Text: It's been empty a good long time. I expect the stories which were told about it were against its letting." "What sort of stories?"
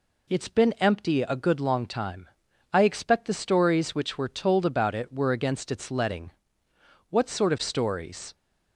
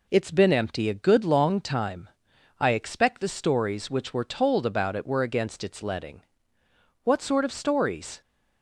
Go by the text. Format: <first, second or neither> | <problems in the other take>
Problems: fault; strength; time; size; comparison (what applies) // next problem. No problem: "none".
neither | none